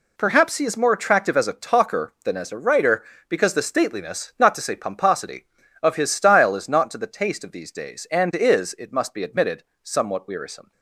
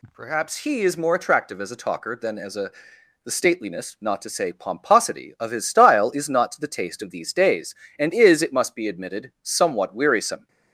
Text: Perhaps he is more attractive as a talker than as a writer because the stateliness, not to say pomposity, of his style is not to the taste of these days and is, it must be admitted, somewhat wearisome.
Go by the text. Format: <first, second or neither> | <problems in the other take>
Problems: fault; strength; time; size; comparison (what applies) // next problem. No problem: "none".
first | skips "writer because"; at 2.9 s